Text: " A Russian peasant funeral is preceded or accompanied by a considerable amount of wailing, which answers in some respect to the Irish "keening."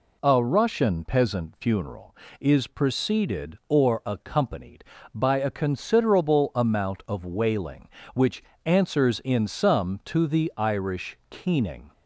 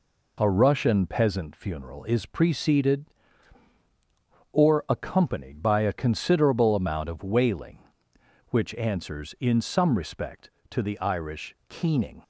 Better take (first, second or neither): second